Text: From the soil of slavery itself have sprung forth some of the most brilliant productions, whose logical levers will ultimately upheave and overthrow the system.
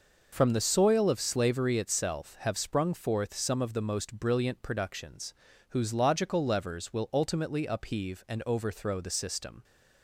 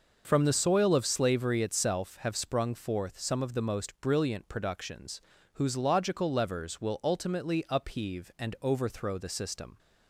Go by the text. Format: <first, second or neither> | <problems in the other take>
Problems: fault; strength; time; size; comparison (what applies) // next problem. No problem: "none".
neither | none